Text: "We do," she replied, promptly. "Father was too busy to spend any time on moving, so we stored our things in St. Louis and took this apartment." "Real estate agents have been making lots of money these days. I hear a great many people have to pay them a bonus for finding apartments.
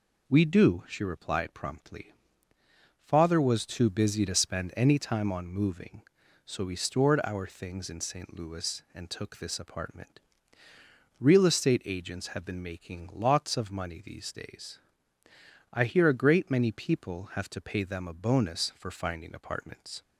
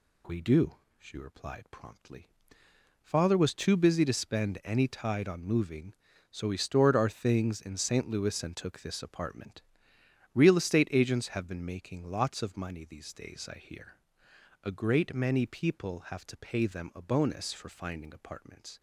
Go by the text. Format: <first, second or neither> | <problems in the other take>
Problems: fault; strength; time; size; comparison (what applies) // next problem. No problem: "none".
first | says "tide" for "time"; at 4.8 s // pauses between "hear" and "a"; noticeable; at 13.9 s; 0.64 s long